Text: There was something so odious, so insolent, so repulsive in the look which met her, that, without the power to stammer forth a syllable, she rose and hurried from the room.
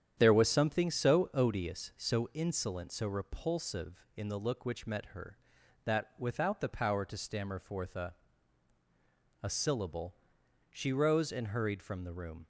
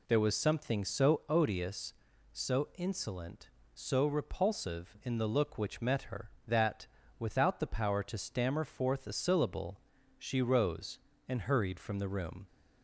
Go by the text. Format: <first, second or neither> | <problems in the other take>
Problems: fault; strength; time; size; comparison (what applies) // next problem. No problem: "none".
second | starts louder than the rest; strong; until 1.1 s; 9.5 dB // says "a" twice; at 9.4 s